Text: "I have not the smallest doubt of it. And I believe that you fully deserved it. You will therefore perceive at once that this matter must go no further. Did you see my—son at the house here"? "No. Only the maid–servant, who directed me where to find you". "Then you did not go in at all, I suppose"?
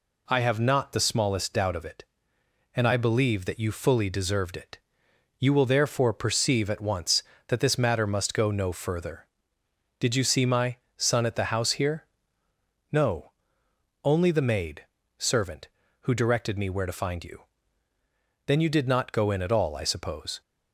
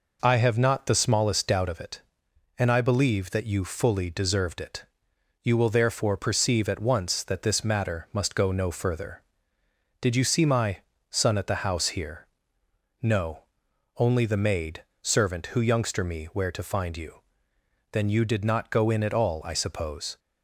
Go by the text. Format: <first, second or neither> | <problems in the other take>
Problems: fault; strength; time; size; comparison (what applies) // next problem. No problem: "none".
first | says "youngster" for "directed"; at 15.6 s